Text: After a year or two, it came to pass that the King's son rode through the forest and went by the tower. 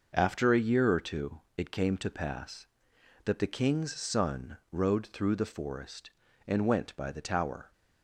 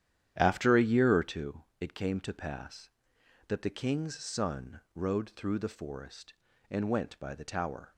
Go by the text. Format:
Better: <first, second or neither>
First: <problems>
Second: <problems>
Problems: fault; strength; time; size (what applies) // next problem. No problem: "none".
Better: first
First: none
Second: starts louder than the rest; strong; until 1.5 s; 10.5 dB